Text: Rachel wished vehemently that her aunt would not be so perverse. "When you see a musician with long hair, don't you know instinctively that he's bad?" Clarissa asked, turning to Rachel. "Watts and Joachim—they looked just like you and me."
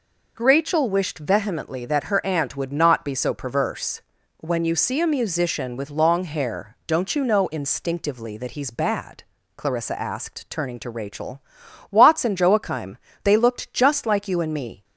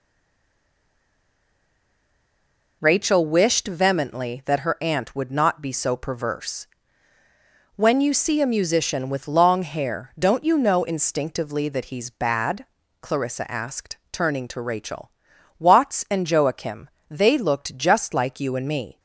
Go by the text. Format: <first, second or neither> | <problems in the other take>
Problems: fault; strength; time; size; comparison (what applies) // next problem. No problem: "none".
first | stays silent before the first word; strong; until 2.8 s; 2.8 s long